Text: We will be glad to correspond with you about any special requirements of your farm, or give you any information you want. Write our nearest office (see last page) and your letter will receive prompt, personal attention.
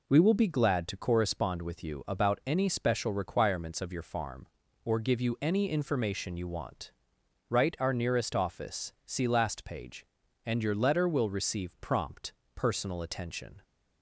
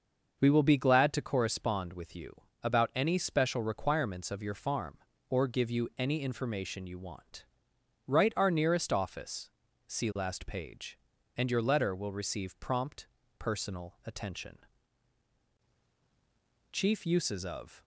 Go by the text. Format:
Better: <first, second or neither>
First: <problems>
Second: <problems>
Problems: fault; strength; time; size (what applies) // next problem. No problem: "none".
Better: first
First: none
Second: starts louder than the rest; until 1.4 s; 6 dB // pauses between "you" and "about"; slight; at 2.3 s; 0.28 s long // goes on to say "Chief Uses of"; noticeable; from 16.7 s on; 1.1 s long